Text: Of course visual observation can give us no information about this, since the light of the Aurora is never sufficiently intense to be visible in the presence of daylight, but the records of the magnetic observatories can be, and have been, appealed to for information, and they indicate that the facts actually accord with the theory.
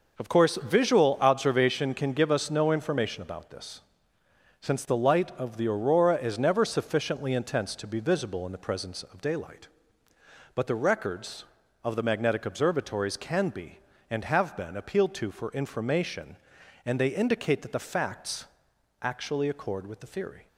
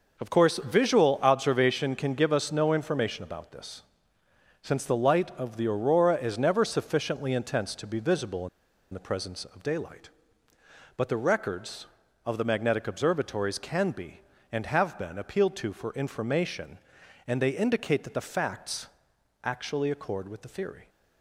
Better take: first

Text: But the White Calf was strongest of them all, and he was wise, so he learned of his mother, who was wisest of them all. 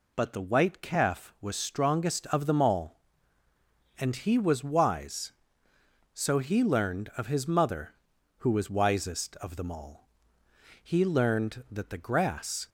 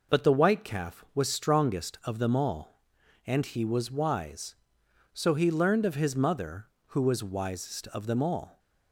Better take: second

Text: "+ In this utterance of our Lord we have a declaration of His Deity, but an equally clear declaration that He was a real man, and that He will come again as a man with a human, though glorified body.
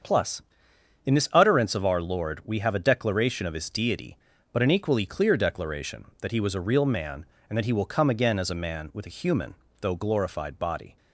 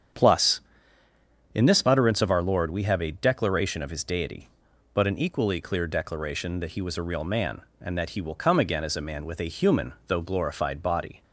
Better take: neither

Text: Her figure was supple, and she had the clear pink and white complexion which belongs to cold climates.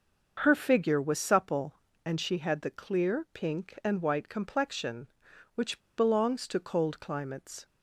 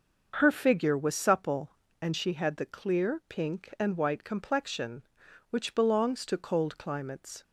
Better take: second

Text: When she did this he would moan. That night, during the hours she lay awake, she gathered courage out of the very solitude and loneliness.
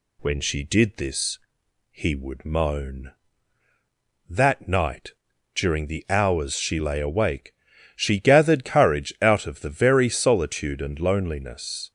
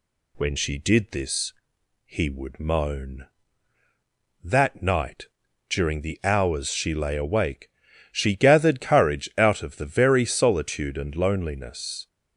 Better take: neither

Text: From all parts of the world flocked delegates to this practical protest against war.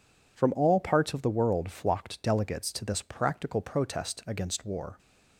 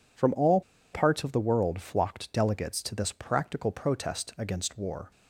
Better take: first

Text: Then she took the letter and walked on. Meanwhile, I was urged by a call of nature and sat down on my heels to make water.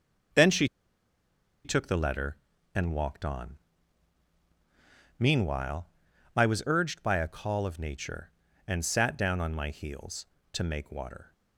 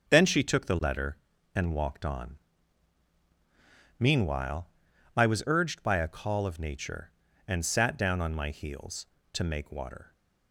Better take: second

